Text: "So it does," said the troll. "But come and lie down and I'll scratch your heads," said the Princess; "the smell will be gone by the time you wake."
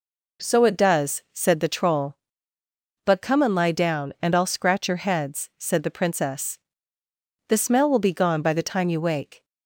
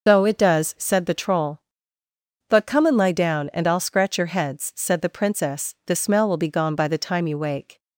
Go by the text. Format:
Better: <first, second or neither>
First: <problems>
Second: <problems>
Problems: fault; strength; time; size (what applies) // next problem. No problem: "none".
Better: first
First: none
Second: loses the start of "So"; at 0.0 s; 155 ms // starts louder than the rest; noticeable; until 1.1 s; 6 dB